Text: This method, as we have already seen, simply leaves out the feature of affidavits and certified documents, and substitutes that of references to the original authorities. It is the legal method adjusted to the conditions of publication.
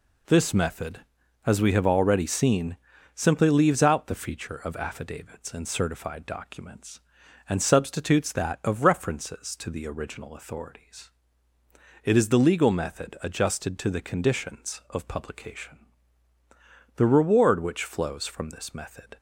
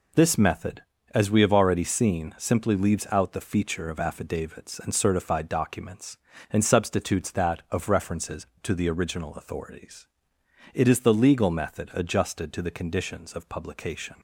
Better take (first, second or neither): second